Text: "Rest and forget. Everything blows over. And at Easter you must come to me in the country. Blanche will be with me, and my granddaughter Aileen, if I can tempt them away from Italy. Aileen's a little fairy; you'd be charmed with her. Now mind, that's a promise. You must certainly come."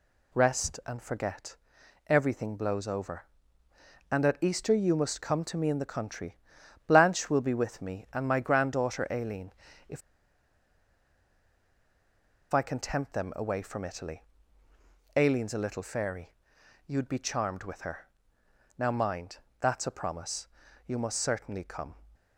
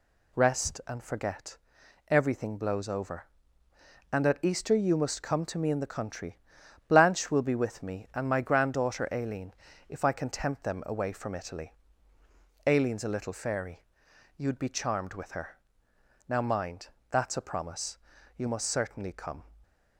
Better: second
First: pauses between "if" and "I"; strong; at 10.0 s; 2.5 s long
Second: none

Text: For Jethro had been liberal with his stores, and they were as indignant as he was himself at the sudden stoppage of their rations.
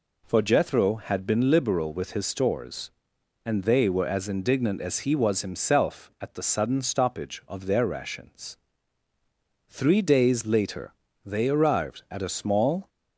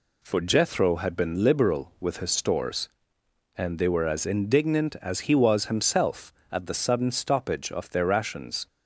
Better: second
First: goes on to say "Three days later they arrived at a small"; strong; from 9.6 s on; 3.2 s long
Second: none

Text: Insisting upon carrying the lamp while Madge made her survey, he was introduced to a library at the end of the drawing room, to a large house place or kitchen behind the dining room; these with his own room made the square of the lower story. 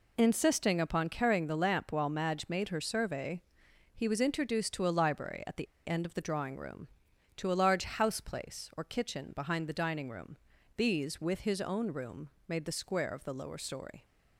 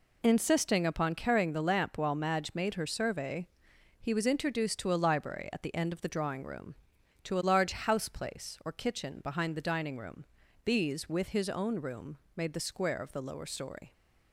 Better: second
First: pauses between "the" and "end"; slight; at 5.6 s; 0.19 s long // pauses between "room" and "made"; slight; at 12.3 s; 0.18 s long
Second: pauses between "room" and "made"; slight; at 12.1 s; 0.18 s long

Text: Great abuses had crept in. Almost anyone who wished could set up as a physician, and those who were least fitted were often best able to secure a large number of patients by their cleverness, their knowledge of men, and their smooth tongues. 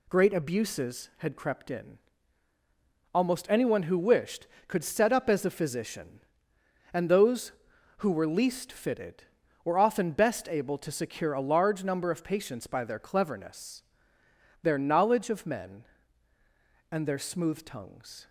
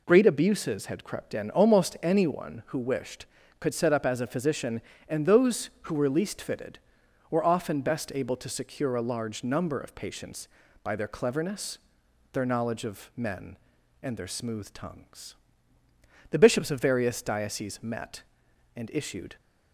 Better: first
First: none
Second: goes on to say "The bishops of various dioceses met and issued"; strong; from 16.3 s on; 3.0 s long

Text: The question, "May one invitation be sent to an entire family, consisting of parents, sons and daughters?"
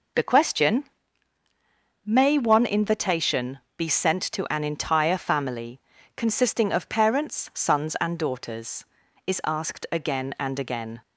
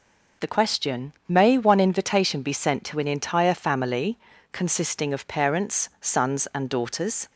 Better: second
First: pauses between "invitation" and "be"; slight; at 3.5 s; 0.20 s long // goes on to say "is asked again and again"; strong; from 9.2 s on; 1.7 s long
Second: none

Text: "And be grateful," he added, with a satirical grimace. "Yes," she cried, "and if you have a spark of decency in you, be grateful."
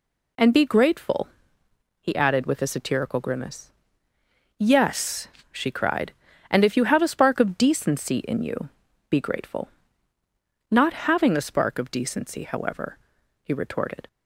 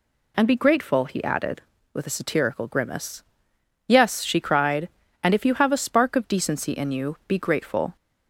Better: second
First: goes on to say "Not having a spark of decency however he retorted"; strong; from 10.7 s on; 3.3 s long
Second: none

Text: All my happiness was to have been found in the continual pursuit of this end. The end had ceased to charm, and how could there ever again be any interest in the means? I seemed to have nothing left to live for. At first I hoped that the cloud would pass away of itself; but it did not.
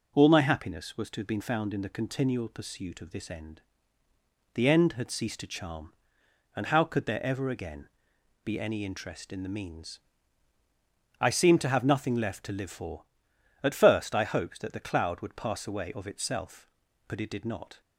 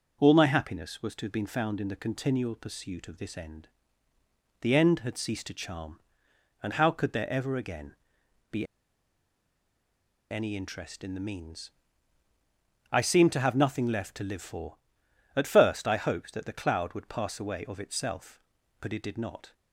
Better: first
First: pauses between "again" and "be"; noticeable; at 7.8 s; 0.56 s long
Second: pauses between "again" and "be"; noticeable; at 7.9 s; 0.56 s long // pauses between "be" and "any"; strong; at 8.6 s; 1.6 s long

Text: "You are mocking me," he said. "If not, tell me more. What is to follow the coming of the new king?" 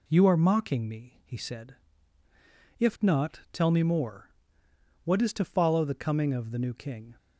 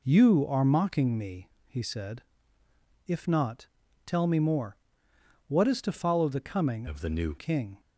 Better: first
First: none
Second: changes voice from "of" to "new"; from 6.8 to 7.3 s; 0.5 s long

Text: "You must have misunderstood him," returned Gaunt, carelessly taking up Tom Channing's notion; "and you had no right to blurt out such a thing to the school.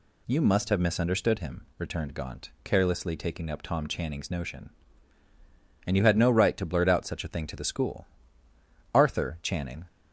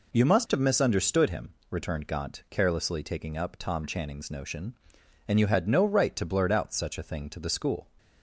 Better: second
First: goes on to say "Arthur Channing"; noticeable; from 8.9 s on; 0.90 s long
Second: none

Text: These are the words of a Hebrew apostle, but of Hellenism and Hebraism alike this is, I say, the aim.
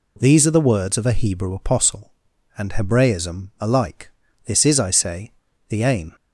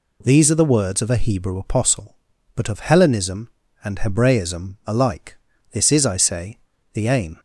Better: second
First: skips "but of Hellenism"; at 2.3 s // pauses between "alike" and "this"; at 4.0 s; 0.38 s long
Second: pauses between "alike" and "this"; at 5.3 s; 0.38 s long

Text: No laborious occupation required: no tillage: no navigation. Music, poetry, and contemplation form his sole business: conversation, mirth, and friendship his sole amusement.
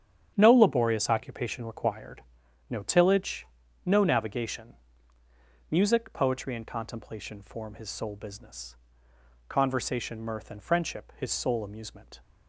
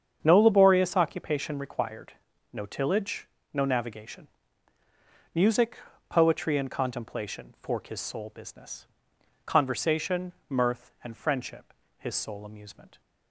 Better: first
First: starts louder than the rest; strong; until 1.3 s; 9 dB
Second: starts louder than the rest; strong; until 1.2 s; 7.5 dB // says "fork" for "form"; at 7.6 s // pauses between "friendship" and "his"; slight; at 11.7 s; 0.26 s long

